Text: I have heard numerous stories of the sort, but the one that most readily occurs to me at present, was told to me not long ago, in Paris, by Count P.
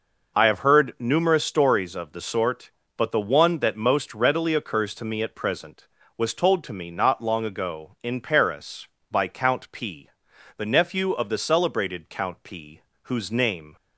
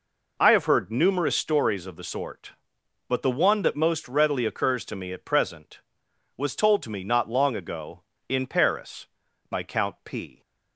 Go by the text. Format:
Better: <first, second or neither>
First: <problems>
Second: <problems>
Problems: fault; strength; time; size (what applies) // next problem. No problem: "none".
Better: second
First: goes on to say "the nephew of the celebrated Count P whose name"; strong; from 10.5 s on; 3.2 s long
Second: none